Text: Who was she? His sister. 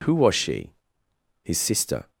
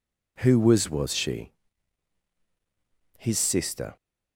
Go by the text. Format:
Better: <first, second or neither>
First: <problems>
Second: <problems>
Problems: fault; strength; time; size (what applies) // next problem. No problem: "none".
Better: first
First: none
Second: says "was" twice; at 0.8 s